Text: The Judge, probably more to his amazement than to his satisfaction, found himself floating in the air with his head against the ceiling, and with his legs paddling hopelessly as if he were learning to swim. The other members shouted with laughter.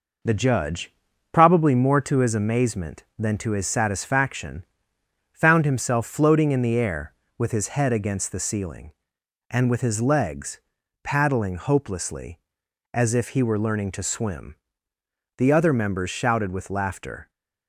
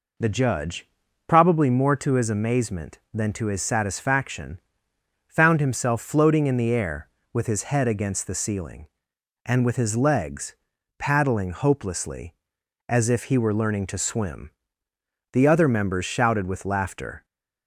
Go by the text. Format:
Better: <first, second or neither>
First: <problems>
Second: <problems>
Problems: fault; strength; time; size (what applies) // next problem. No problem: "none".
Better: second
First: gets quieter; throughout; 3.5 dB // pauses between "legs" and "paddling"; at 10.5 s; 0.44 s long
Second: pauses between "legs" and "paddling"; at 10.5 s; 0.44 s long